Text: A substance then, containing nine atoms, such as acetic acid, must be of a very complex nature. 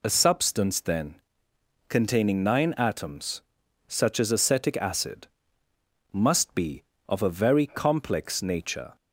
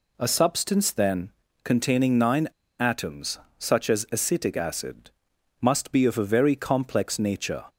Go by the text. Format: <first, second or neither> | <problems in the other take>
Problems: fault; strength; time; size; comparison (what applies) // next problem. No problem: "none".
first | pauses between "nine" and "atoms"; slight; at 2.4 s; 0.32 s long